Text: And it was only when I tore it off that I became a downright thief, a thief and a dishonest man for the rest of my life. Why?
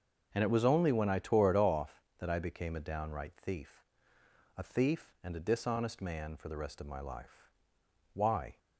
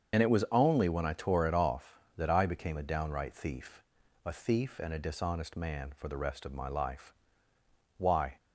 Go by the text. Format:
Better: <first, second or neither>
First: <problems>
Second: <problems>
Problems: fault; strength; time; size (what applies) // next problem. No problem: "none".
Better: first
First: starts louder than the rest; until 1.3 s; 6.5 dB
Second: loses the start of "And"; at 0.1 s; 40 ms // starts louder than the rest; until 1.2 s; 7 dB